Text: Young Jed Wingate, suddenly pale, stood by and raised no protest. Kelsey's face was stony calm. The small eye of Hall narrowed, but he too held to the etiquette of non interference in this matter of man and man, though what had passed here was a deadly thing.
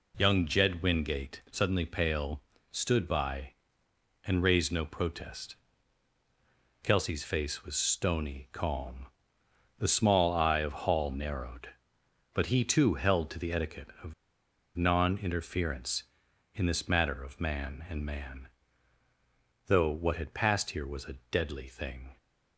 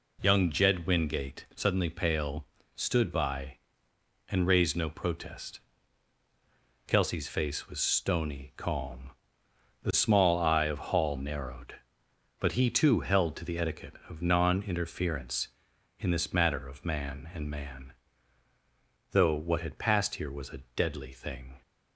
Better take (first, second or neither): second